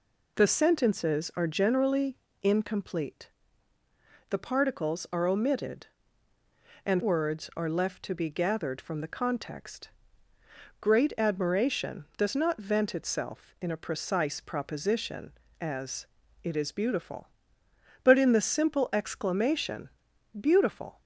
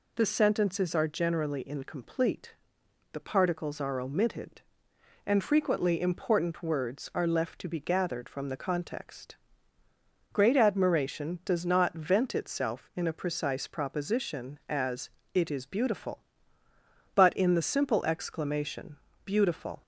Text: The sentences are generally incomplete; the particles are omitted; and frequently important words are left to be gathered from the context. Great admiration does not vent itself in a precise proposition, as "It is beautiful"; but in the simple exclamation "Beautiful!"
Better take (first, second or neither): second